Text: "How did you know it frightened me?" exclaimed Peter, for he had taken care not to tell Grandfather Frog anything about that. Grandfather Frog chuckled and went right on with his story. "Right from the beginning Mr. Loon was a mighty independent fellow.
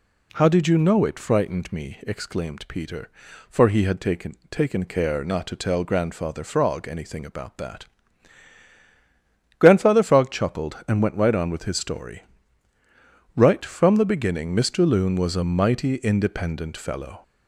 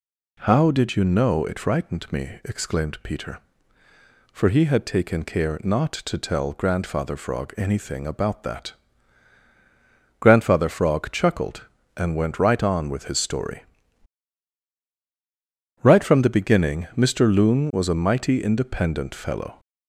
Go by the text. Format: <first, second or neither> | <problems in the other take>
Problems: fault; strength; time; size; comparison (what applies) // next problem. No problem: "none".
second | says "taken" twice; at 4.4 s